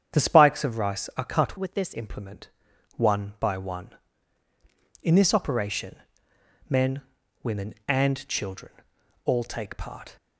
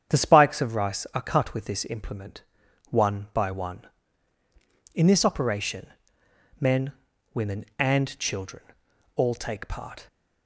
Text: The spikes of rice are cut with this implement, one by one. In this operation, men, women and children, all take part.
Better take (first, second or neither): second